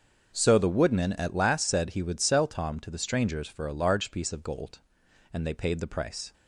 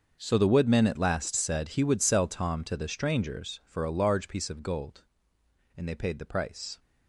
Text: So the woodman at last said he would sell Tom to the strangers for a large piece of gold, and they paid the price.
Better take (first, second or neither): first